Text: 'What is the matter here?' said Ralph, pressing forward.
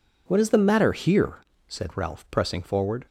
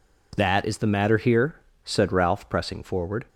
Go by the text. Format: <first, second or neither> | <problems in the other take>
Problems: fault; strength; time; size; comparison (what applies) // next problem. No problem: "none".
first | says "That" for "What"; at 0.3 s